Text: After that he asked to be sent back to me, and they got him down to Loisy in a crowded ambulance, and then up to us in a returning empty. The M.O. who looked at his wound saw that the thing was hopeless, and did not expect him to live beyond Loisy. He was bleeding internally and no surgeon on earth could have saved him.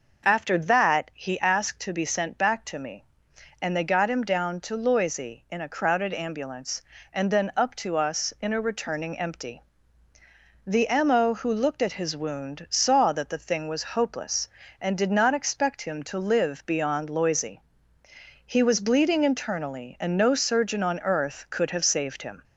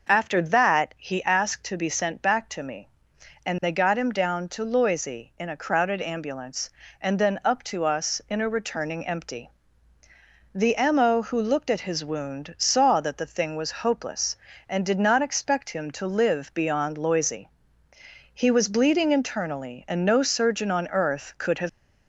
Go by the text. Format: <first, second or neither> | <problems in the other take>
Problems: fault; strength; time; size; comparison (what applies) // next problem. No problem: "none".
first | stops before "saved him"; at 21.6 s